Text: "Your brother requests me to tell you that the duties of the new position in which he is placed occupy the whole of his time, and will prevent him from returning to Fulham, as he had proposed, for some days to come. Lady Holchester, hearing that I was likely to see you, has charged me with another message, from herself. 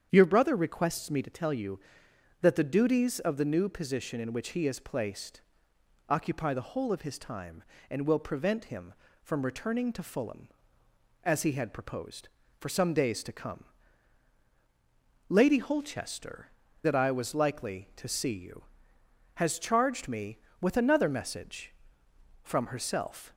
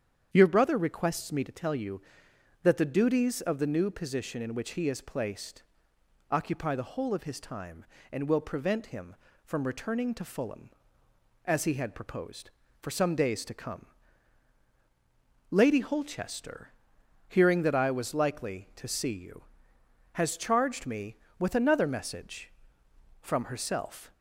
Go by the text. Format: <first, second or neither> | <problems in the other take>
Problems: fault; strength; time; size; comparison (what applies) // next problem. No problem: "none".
second | starts louder than the rest; strong; until 1.1 s; 8.5 dB; strong in the second // pauses between "placed" and "occupy"; noticeable; at 5.4 s; 0.66 s long; noticeable in the second // skips "hearing"; at 16.6 s